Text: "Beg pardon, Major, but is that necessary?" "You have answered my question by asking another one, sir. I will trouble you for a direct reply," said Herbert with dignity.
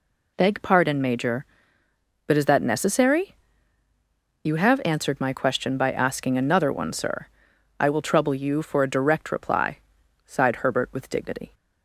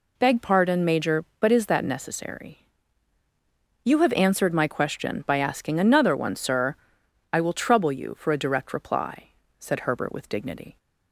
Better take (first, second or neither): second